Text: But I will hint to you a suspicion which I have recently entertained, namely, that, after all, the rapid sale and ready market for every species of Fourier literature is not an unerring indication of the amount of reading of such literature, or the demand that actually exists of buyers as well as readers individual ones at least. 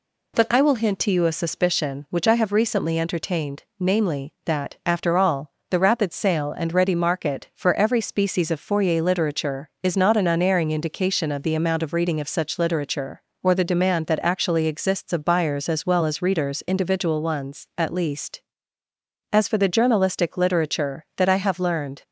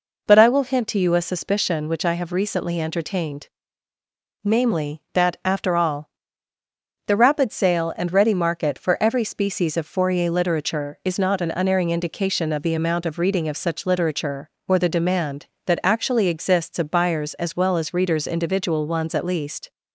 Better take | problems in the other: second | goes on to say "As for the journalistic literature that I have learned"; strong; from 19.3 s on; 2.7 s long

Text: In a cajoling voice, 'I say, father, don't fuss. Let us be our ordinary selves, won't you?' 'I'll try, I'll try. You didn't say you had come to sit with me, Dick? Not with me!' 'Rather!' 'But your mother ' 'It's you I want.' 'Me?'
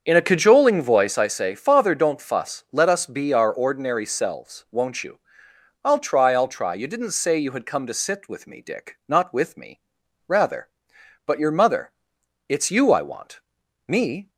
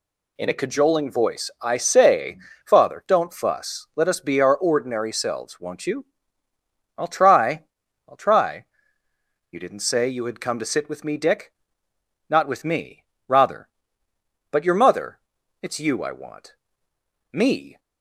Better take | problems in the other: second | starts louder than the rest; strong; until 1.3 s; 7 dB

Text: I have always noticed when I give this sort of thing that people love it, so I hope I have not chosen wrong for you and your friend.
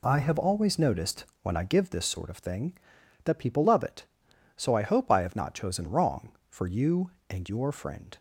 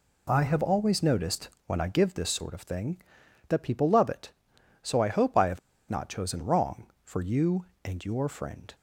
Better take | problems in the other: first | pauses between "noticed" and "when"; slight; at 1.4 s; 0.16 s long; slight in the first // pauses between "have" and "not"; slight; at 5.5 s; 0.31 s long

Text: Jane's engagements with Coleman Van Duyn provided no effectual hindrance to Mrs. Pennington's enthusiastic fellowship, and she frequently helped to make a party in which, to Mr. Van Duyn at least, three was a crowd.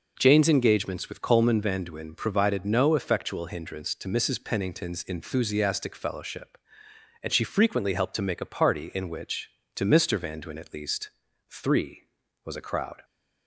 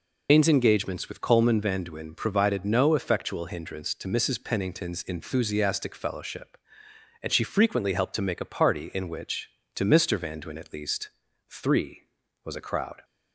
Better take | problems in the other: first | loses the start of "Jane's"; at 0.2 s; 130 ms

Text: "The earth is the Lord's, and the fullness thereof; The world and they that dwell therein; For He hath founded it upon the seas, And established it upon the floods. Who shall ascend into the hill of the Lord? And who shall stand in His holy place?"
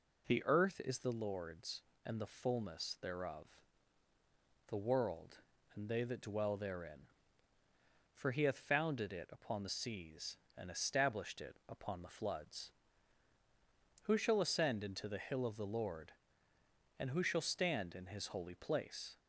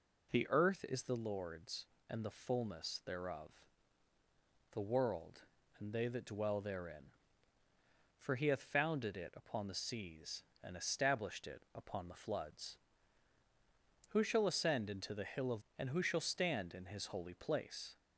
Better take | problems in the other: first | skips "the Lord"; at 15.6 s

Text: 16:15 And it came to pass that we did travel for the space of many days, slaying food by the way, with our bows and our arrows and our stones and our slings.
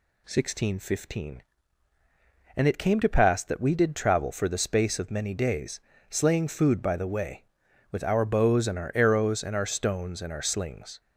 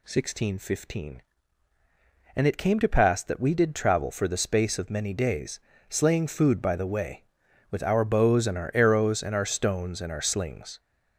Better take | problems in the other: first | gets louder; noticeable; throughout; 5.5 dB

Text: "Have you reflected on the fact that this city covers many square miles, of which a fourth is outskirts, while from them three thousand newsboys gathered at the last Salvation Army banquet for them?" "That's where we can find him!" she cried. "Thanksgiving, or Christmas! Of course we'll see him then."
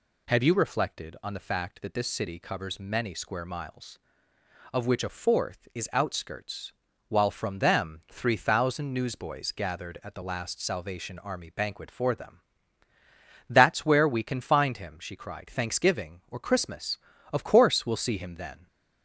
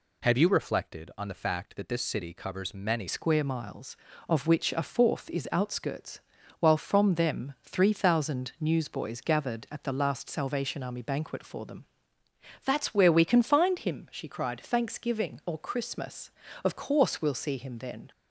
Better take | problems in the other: first | changes voice at "square"; from 3.0 s on; 15.1 s long

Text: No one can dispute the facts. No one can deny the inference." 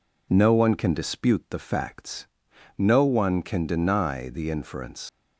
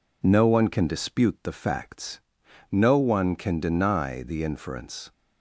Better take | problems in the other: second | leaves "inference" unfinished; at 5.0 s; 90 ms

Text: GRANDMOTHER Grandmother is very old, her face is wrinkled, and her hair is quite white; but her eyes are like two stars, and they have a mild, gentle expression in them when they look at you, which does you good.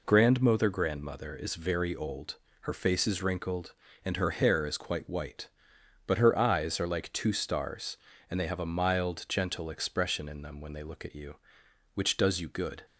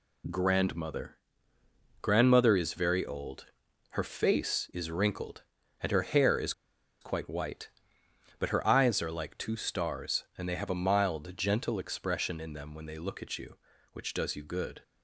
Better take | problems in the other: first | pauses between "GRANDMOTHER" and "Grandmother"; noticeable; at 1.1 s; 0.84 s long // pauses between "is" and "quite"; noticeable; at 6.5 s; 0.49 s long

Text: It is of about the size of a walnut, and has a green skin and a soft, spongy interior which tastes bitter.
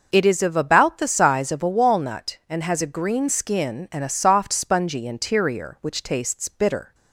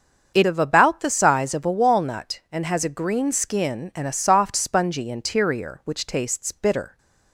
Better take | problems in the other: first | starts louder than the rest; until 1.3 s; 7 dB // skips "is"; at 0.4 s

